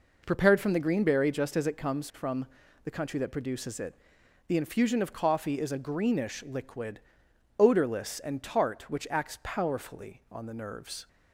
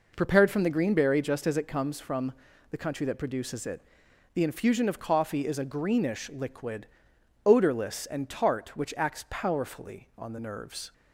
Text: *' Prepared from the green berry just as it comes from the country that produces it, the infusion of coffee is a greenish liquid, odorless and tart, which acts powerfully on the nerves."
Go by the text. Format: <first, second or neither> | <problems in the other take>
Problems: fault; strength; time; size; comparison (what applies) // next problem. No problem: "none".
neither | pauses between "from" and "the"; the same in both